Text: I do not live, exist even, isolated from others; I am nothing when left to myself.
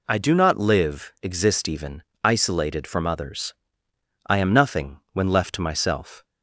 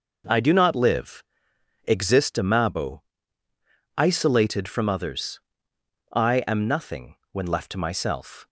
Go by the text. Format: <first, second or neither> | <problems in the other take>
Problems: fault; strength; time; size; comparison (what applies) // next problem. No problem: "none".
first | says "amabo" for "even"; at 2.3 s // pauses between "nothing" and "when"; slight; at 7.1 s; 0.18 s long; slight in the first